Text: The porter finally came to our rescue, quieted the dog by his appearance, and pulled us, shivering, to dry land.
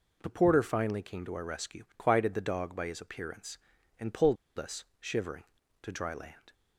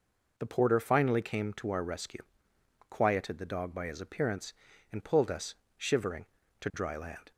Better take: second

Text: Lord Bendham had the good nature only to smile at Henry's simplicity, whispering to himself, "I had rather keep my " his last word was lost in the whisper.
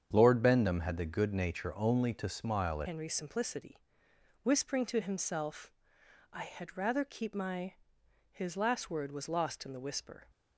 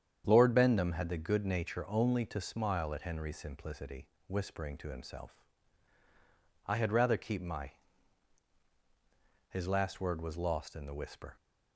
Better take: second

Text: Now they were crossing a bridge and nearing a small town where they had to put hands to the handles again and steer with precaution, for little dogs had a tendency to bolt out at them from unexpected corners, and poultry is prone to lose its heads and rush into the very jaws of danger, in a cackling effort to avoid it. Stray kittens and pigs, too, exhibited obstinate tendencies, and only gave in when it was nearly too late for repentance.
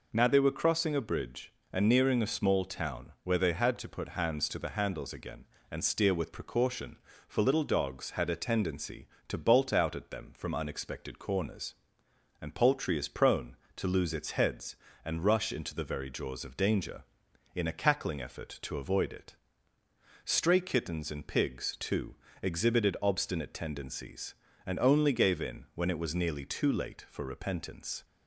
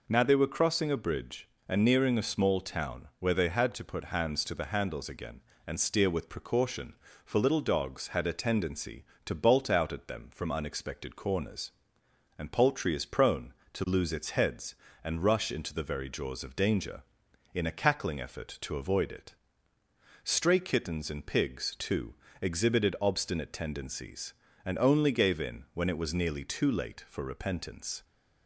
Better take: neither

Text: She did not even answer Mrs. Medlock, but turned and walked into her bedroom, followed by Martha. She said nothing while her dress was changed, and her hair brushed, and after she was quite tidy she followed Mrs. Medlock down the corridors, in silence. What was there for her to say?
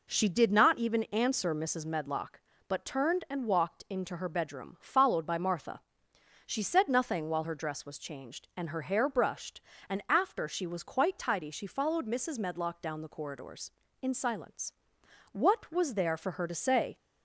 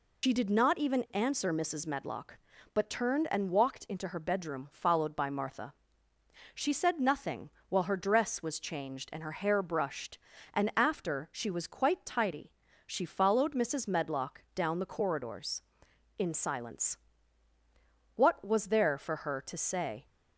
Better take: first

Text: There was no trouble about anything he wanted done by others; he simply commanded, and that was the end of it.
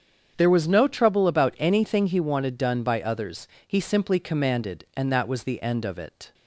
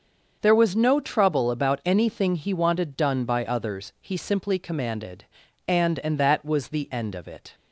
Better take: first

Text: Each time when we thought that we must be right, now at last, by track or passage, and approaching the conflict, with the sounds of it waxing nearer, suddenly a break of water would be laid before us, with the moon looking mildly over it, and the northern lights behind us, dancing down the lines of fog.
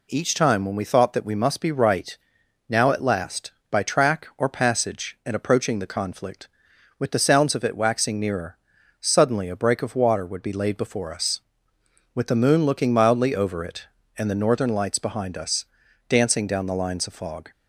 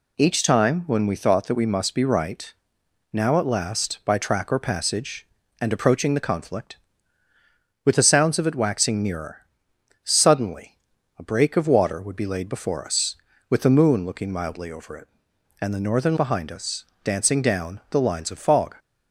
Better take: first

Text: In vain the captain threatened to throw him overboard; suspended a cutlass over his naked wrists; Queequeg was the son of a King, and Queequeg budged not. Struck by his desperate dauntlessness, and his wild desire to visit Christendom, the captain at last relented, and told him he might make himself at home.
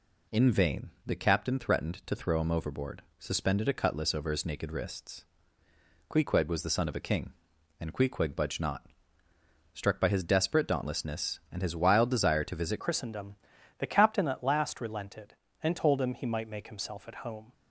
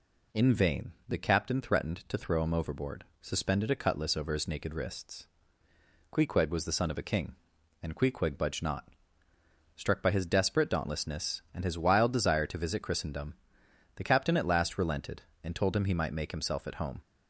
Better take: second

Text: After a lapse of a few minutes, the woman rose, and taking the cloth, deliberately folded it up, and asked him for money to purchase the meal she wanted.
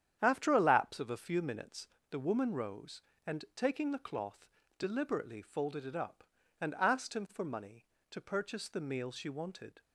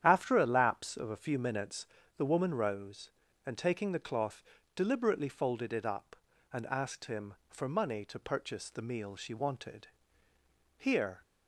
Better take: first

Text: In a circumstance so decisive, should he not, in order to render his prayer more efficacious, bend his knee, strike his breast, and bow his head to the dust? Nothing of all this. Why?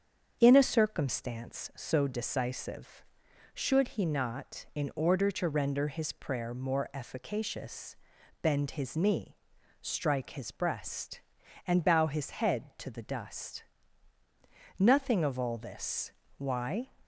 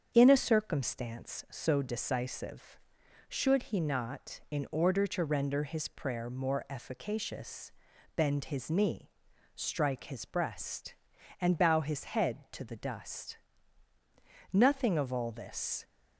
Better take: first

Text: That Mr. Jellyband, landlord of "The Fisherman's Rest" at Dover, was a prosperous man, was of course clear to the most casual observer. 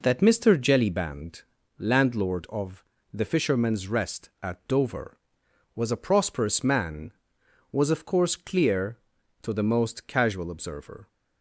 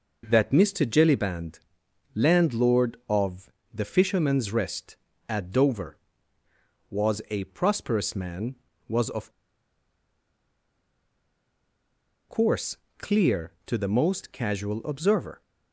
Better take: first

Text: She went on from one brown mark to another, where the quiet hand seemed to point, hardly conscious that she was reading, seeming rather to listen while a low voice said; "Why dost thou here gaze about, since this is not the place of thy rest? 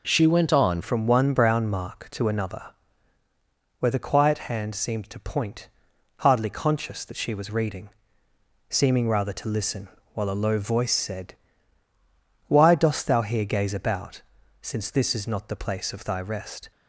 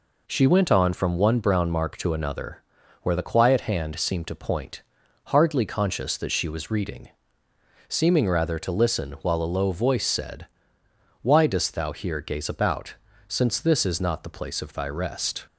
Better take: second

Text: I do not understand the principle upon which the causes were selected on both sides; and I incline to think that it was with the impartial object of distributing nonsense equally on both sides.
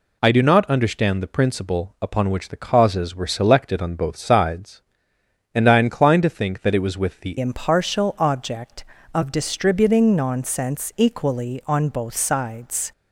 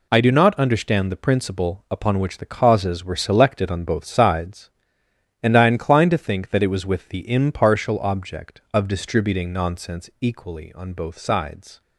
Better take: second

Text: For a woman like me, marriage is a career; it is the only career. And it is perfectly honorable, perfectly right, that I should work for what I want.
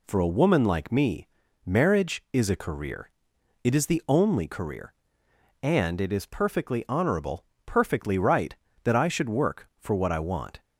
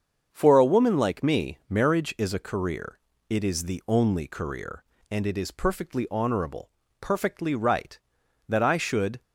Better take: first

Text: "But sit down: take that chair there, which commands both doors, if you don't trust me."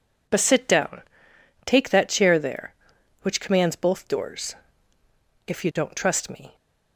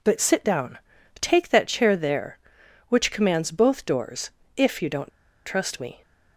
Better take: first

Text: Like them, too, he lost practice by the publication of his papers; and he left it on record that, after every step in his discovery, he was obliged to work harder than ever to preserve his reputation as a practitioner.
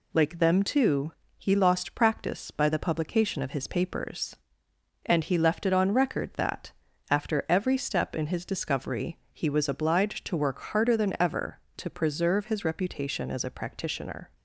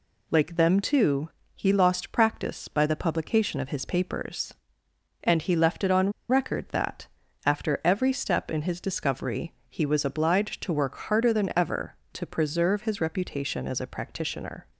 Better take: first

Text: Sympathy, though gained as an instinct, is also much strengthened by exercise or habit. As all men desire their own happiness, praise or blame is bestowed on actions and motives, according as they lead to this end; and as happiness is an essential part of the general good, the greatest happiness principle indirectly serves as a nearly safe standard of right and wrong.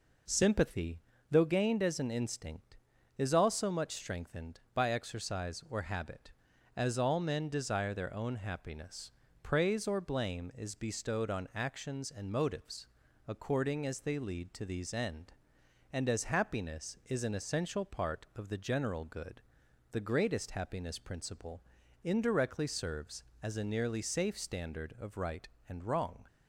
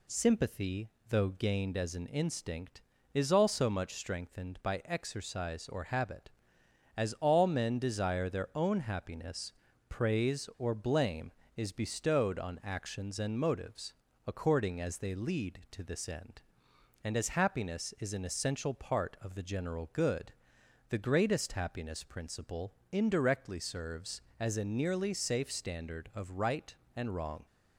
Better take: second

